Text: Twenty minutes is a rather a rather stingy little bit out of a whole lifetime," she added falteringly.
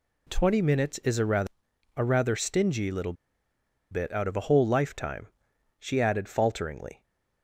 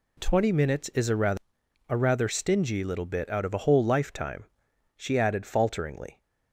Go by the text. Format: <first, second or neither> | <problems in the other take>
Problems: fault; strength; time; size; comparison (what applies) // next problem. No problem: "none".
second | pauses between "rather" and "a"; noticeable; at 1.4 s; 0.48 s long; noticeable in the second // pauses between "little" and "bit"; noticeable; at 3.1 s; 0.77 s long